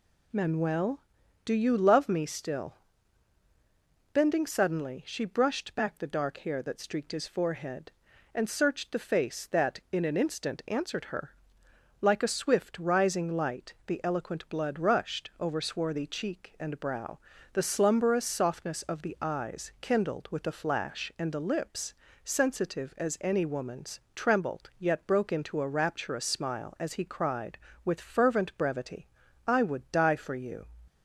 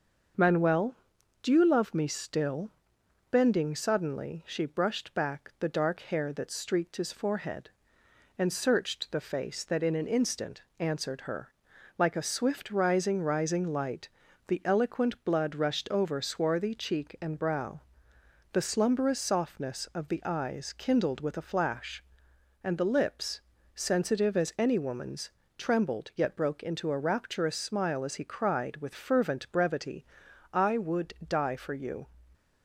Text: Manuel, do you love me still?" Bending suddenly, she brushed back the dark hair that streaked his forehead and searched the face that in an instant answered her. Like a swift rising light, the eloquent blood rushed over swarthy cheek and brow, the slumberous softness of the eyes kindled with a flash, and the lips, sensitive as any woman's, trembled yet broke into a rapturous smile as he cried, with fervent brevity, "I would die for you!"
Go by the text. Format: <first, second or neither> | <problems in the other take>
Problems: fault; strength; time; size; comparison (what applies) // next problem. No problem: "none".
first | starts louder than the rest; until 1.8 s; 6.5 dB // pauses between "instant" and "answered"; slight; at 10.6 s; 0.16 s long // says "rising" twice; at 13.2 s